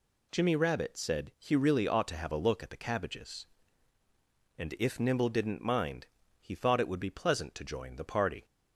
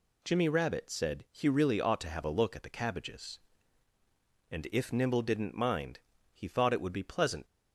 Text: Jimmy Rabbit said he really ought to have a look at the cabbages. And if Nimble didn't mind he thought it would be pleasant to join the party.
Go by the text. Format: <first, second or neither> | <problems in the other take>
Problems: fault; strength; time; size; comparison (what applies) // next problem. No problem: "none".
first | pauses between "mind" and "he"; slight; at 5.9 s; 0.34 s long; slight in the first // stops before "to join the party"; at 7.4 s